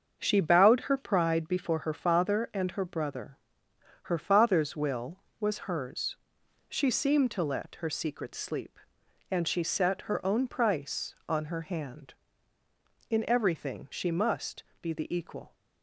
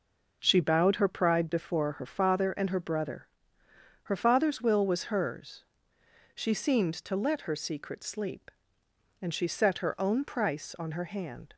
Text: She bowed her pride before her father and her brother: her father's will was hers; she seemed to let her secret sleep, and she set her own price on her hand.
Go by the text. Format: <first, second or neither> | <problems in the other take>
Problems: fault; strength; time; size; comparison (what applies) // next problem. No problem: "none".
second | starts louder than the rest; until 1.2 s; 7 dB // goes on to say "In everything she must be the equal"; strong; from 13.0 s on; 2.4 s long